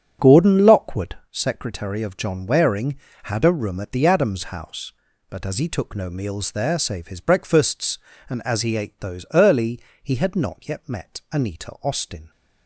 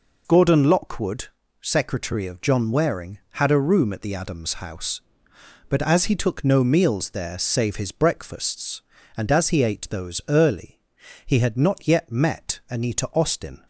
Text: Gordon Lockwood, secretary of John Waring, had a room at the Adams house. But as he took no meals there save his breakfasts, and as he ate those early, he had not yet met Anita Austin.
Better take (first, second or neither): second